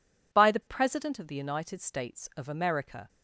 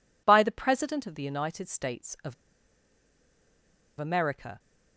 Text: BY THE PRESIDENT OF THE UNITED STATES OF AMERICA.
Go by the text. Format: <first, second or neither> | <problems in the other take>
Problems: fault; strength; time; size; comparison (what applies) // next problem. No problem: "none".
first | pauses between "OF" and "AMERICA"; strong; at 2.3 s; 1.6 s long